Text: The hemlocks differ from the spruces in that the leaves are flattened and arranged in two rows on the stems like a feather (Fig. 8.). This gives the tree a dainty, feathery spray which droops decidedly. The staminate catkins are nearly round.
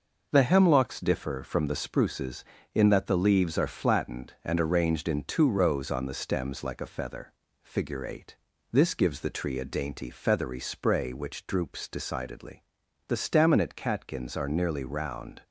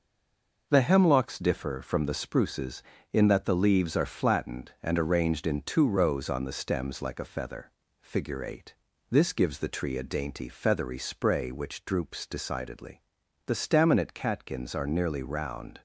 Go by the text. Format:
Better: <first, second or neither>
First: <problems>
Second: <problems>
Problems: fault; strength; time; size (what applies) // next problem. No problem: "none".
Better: first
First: none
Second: stays silent before the first word; slight; until 0.6 s; 0.6 s long